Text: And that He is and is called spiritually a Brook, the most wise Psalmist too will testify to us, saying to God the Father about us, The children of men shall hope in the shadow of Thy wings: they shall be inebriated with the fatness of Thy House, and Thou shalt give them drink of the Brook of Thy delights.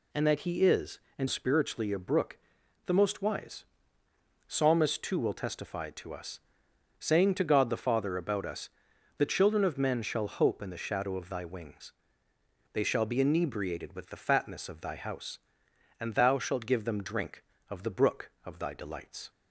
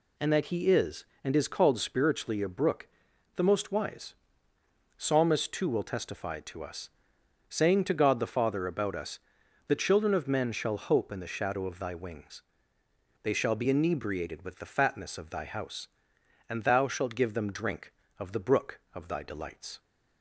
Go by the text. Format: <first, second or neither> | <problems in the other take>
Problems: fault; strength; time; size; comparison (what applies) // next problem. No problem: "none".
second | skips "is called"; at 1.2 s // pauses between "wise" and "Psalmist"; noticeable; at 3.6 s; 0.82 s long; noticeable in the second